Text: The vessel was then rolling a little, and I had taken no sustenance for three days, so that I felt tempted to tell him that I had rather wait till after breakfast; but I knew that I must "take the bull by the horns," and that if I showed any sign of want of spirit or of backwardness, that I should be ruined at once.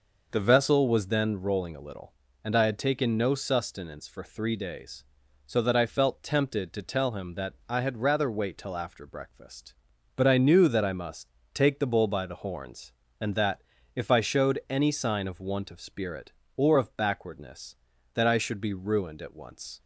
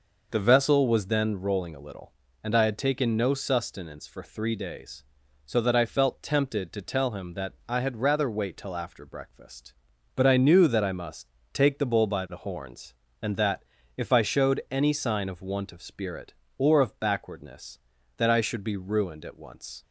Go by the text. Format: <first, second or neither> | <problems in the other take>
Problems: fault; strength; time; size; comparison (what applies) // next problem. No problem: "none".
neither | pauses between "must" and "take"; slight; the same in both // pauses between "that" and "if"; slight; the same in both